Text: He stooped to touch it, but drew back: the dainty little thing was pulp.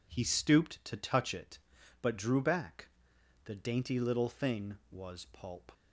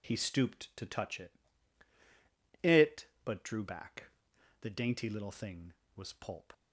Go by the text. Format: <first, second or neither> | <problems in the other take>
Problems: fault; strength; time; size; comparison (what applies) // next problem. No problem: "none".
first | says "it" twice; at 2.6 s